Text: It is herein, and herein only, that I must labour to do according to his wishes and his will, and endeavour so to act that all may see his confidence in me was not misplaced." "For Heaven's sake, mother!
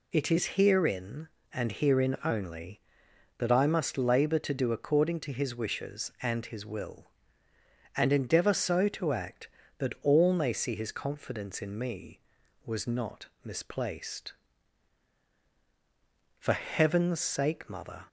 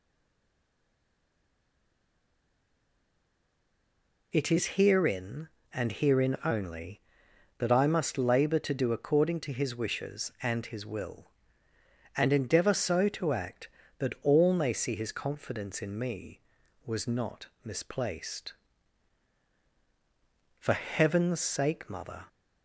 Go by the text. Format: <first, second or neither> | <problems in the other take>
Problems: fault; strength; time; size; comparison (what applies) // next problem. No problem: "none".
first | stays silent before the first word; strong; until 4.3 s; 4.3 s long // pauses between "not" and "misplaced"; slight; at 17.4 s; 0.16 s long; slight in the first